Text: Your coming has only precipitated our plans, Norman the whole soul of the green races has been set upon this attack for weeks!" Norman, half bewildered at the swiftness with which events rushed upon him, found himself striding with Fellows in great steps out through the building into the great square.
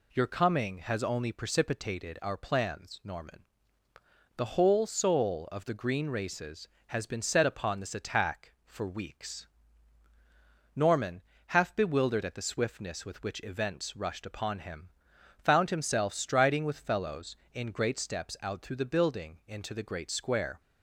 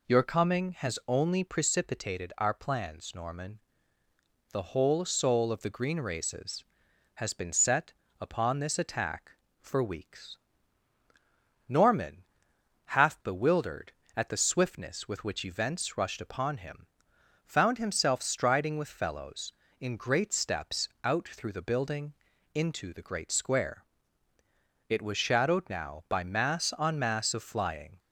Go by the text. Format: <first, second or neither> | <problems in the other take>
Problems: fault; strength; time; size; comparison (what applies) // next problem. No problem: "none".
first | pauses between "Norman" and "the"; noticeable; at 3.5 s; 0.92 s long; noticeable in the first // pauses between "set" and "upon"; slight; at 7.9 s; 0.30 s long // pauses between "steps" and "out"; slight; at 20.8 s; 0.16 s long // pauses between "building" and "into"; at 22.1 s; 0.40 s long // goes on to say "It was shadowed now by mass on mass of flying"; strong; from 24.8 s on; 3.1 s long